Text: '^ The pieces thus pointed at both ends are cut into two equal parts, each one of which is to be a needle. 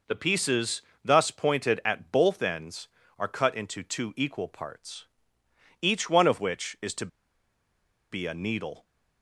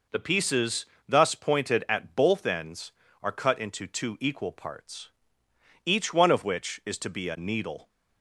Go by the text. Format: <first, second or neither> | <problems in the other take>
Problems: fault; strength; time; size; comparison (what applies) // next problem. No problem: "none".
second | pauses between "pieces" and "thus"; slight; at 0.8 s; 0.20 s long; slight in the second // pauses between "to" and "be"; at 7.0 s; 1.0 s long